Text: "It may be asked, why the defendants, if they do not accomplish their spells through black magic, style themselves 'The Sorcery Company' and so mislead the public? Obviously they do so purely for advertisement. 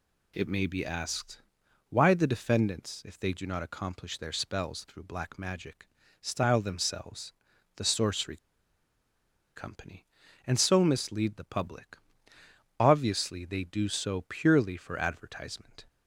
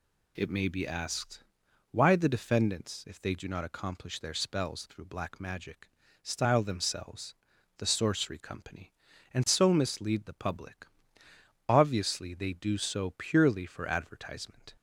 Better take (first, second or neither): second